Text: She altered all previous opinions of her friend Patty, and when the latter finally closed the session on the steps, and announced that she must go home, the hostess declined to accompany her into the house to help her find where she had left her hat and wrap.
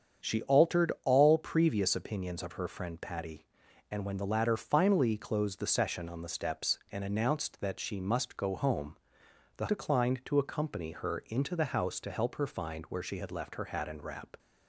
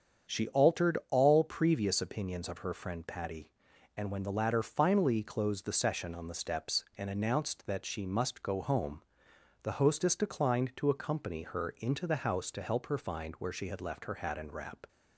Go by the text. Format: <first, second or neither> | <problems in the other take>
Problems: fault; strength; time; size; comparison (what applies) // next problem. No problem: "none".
second | starts louder than the rest; strong; until 1.3 s; 7.5 dB; strong in the second // skips "hostess"; at 9.6 s